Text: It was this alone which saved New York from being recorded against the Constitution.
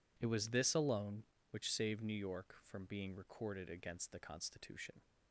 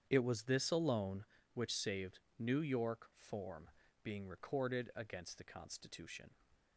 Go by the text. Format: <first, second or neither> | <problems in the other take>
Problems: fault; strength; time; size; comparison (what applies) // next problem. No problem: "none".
first | starts louder than the rest; strong; until 1.0 s; 8.5 dB // pauses between "saved" and "New"; slight; at 2.1 s; 0.18 s long // says "form" for "from"; at 3.1 s